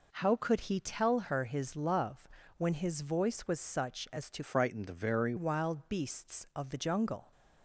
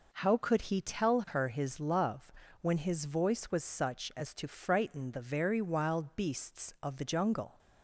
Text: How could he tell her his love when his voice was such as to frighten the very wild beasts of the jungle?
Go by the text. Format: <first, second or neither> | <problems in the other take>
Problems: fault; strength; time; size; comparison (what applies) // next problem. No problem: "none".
second | pauses between "love" and "when"; slight; at 2.2 s; 0.28 s long; slight in the second // changes voice from "frighten" to "very"; from 4.4 to 5.3 s; 0.9 s long